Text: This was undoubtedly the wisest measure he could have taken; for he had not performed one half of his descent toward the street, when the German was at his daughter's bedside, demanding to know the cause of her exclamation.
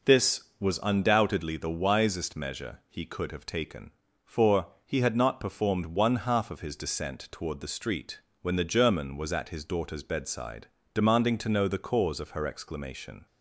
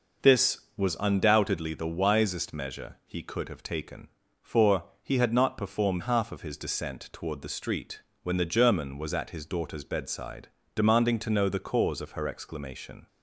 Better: first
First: pauses between "for" and "he"; slight; at 4.6 s; 0.18 s long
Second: pauses between "for" and "he"; slight; at 4.8 s; 0.18 s long // skips "one"; at 6.0 s

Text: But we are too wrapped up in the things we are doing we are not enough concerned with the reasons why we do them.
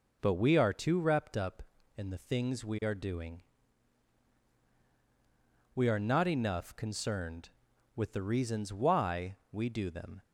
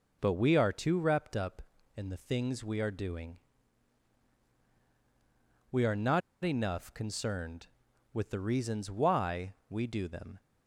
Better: first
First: pauses between "doing" and "we"; strong; at 3.4 s; 2.3 s long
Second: pauses between "doing" and "we"; strong; at 3.3 s; 2.3 s long // pauses between "not" and "enough"; slight; at 6.2 s; 0.23 s long

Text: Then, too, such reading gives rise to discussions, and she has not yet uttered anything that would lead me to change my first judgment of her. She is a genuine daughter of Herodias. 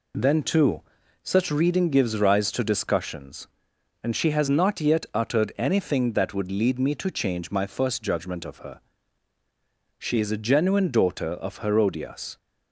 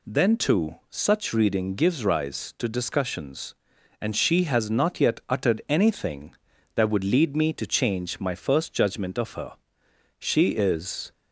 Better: first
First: none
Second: stops before "a genuine daughter of Herodias"; at 11.1 s

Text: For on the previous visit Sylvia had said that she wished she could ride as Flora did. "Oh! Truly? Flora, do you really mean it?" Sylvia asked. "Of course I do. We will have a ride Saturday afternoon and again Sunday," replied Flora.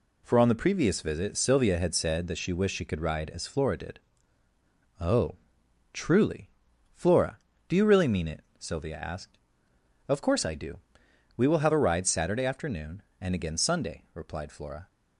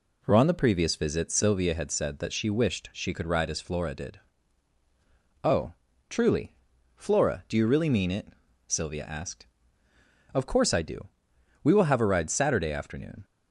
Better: first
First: none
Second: stops before "and again Sunday replied Flora"; at 13.2 s

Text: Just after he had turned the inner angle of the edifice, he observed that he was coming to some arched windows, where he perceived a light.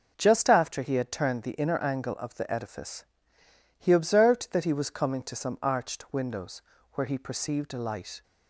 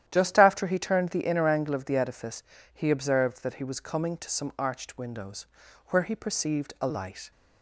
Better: first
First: none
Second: starts louder than the rest; strong; until 1.0 s; 11 dB // skips "had"; at 0.7 s

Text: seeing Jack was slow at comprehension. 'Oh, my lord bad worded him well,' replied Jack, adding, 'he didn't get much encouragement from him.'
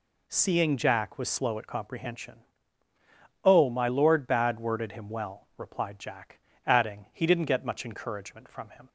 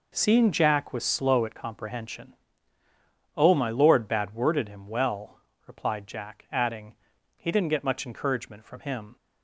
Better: neither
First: none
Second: none

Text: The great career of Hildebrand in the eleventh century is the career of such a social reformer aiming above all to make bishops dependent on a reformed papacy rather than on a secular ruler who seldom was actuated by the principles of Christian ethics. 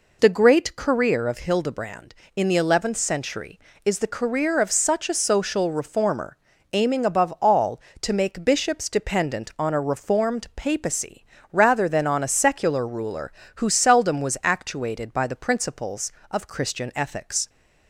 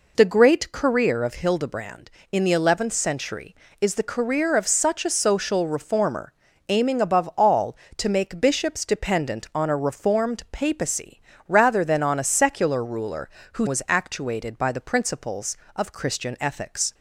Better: first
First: pauses between "reformer" and "aiming"; at 6.3 s; 0.38 s long // pauses between "papacy" and "rather"; slight; at 11.2 s; 0.28 s long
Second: pauses between "reformer" and "aiming"; at 6.3 s; 0.38 s long // pauses between "papacy" and "rather"; slight; at 11.2 s; 0.28 s long // skips "seldom"; at 13.6 s

